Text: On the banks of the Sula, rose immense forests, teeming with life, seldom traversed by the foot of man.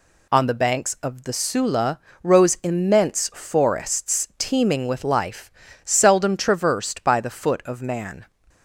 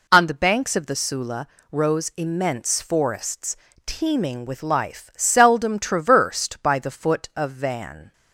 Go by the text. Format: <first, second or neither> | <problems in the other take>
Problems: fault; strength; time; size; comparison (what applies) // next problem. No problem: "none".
first | says "van" for "man"; at 7.5 s